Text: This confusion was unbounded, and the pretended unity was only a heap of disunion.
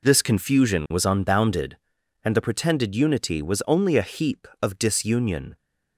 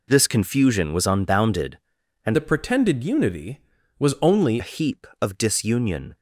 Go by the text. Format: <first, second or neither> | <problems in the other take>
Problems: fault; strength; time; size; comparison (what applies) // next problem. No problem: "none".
first | changes voice from "the" to "only"; from 2.3 to 4.6 s; 2.3 s long